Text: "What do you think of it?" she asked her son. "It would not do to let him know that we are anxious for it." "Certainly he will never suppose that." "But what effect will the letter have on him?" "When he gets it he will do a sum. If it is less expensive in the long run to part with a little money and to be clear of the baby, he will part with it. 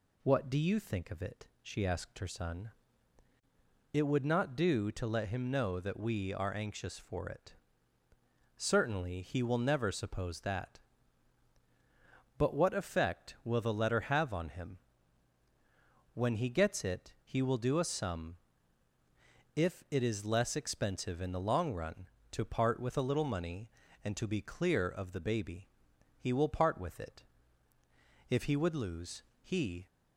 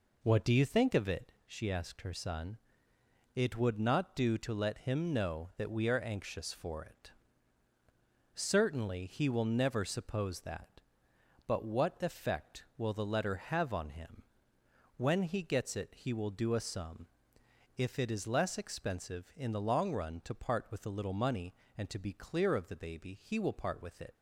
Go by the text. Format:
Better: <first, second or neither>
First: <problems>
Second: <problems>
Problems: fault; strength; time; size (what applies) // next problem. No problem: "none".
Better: second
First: goes on to say "If he would lose he"; from 28.2 s on; 1.5 s long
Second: none